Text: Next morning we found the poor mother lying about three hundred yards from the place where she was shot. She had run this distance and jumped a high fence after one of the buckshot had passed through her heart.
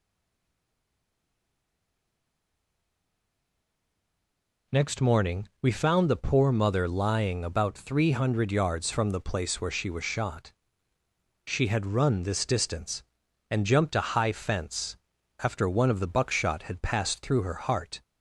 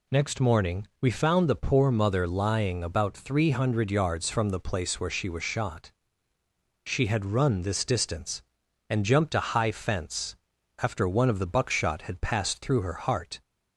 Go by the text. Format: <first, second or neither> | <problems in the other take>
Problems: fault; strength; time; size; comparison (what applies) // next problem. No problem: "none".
second | stays silent before the first word; strong; until 4.7 s; 4.7 s long // pauses between "fence" and "after"; at 14.9 s; 0.44 s long; also in the second